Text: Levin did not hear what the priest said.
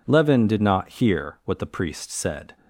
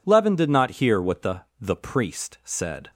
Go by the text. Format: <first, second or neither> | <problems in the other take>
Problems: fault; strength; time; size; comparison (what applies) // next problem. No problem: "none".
first | says "the" twice; at 1.5 s